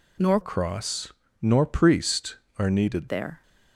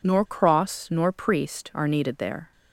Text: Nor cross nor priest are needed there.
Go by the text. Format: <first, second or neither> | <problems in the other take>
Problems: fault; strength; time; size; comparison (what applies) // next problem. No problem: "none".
second | changes voice from "cross" to "needed"; from 0.4 to 3.0 s; 2.6 s long // pauses between "cross" and "nor"; slight; at 1.1 s; 0.30 s long